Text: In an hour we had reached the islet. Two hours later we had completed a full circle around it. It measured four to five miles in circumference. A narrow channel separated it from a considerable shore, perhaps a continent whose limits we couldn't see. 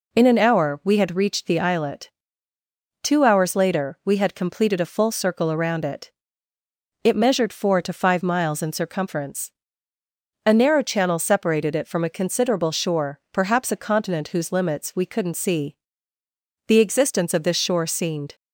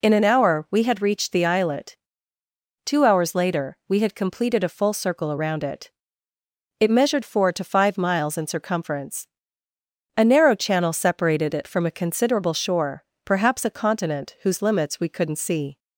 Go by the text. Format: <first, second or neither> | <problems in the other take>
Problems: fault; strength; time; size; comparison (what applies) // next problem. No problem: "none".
second | goes on to say "The existence of this shore seemed"; strong; from 16.6 s on; 1.6 s long